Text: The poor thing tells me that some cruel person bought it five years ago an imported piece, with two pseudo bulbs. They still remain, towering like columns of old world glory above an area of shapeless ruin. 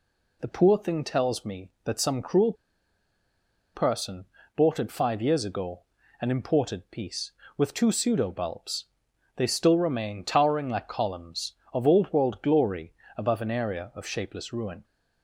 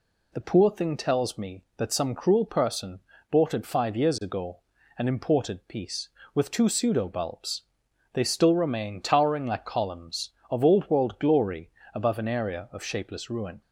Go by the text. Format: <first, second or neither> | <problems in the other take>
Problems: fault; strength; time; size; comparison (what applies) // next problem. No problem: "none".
second | pauses between "cruel" and "person"; at 2.5 s; 1.2 s long // pauses between "person" and "bought"; slight; at 4.2 s; 0.30 s long; slight in the second // pauses between "ago" and "an"; at 5.8 s; 0.40 s long; also in the second // pauses between "glory" and "above"; slight; at 12.9 s; 0.22 s long; slight in the second